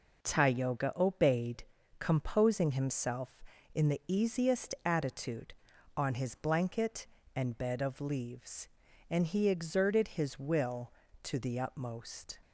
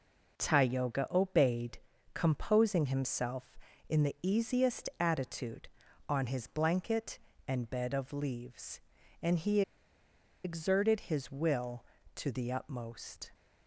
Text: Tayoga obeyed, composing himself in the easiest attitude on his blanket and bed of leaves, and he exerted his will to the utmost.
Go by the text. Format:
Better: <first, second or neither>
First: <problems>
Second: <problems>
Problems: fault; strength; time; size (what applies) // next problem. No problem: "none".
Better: first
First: none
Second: pauses between "he" and "exerted"; noticeable; at 9.6 s; 0.83 s long